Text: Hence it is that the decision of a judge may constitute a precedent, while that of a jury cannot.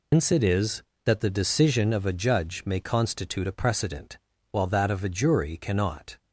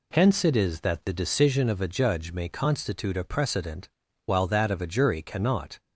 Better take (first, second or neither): second